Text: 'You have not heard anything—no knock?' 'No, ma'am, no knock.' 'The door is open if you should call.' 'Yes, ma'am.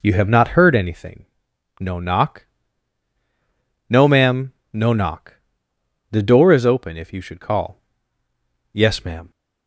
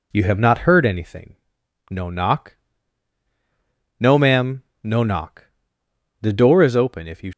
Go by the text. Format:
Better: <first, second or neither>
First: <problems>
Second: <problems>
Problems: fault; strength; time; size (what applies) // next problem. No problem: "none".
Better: first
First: none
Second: stops before "should call Yes ma'am"; at 7.3 s